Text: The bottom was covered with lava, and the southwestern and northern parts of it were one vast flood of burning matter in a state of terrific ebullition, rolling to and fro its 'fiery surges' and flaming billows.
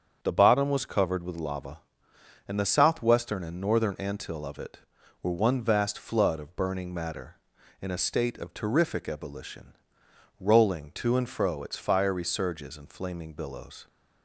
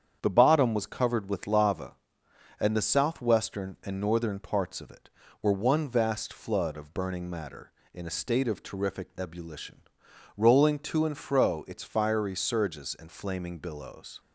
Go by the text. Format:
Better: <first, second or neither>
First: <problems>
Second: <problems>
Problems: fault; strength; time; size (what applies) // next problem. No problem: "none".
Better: second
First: starts louder than the rest; strong; until 1.2 s; 7.5 dB // says "antil" for "parts"; at 3.9 s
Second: starts louder than the rest; strong; until 1.2 s; 8.5 dB